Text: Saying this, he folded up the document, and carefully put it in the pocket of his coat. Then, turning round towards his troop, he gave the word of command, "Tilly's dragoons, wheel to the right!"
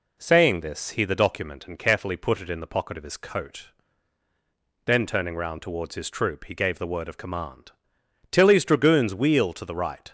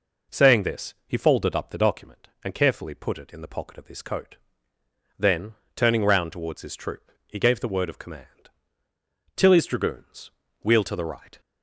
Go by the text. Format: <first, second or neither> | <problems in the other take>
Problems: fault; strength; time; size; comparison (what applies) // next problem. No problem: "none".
second | skips "folded up"; at 1.0 s